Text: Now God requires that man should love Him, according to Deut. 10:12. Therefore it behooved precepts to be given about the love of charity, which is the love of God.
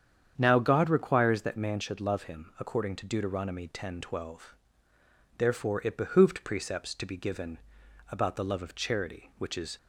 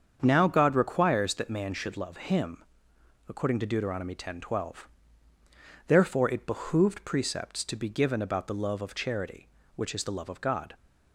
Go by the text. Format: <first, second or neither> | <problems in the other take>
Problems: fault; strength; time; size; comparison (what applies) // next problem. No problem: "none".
second | starts louder than the rest; strong; until 1.3 s; 8.5 dB; strong in the second // pauses between "given" and "about"; noticeable; at 7.5 s; 0.50 s long // stops before "the love of God"; at 9.7 s